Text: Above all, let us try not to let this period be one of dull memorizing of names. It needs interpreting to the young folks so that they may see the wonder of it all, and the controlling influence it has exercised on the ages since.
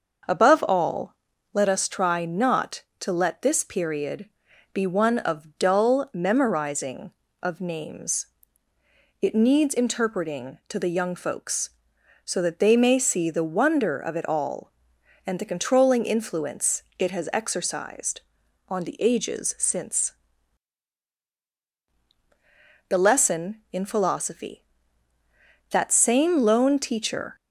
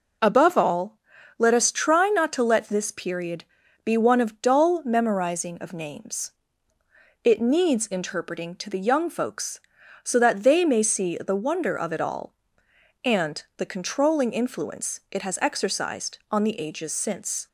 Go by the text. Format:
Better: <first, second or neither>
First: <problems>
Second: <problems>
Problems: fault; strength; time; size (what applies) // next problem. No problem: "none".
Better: second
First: starts louder than the rest; until 1.6 s; 6 dB // pauses between "period" and "be"; noticeable; at 4.2 s; 0.46 s long // goes on to say "The Lesson in Philosophy That same lone teacher"; strong; from 22.8 s on; 4.4 s long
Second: pauses between "period" and "be"; at 3.4 s; 0.40 s long